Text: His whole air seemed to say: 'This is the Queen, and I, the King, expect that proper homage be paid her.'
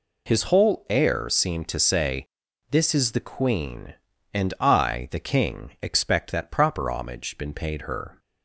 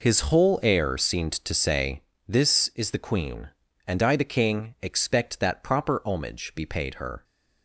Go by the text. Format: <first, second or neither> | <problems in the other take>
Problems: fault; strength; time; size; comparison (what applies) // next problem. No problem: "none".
second | says "been" for "be"; at 7.3 s